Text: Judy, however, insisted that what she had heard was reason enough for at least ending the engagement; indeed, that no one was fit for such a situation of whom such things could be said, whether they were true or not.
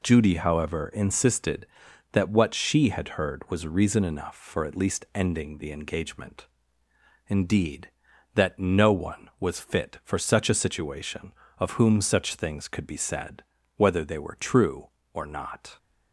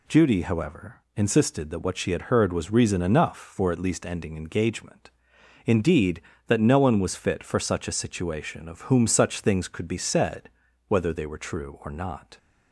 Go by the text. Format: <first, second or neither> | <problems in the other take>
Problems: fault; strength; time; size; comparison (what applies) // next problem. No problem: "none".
first | skips "the"; at 4.3 s